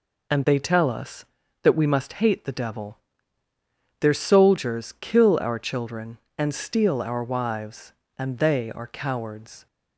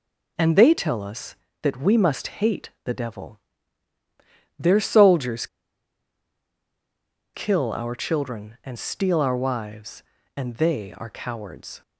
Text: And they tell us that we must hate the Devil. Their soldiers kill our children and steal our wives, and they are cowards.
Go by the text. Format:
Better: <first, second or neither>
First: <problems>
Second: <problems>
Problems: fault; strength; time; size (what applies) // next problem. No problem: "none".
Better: first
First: none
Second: pauses between "soldiers" and "kill"; strong; at 5.4 s; 1.8 s long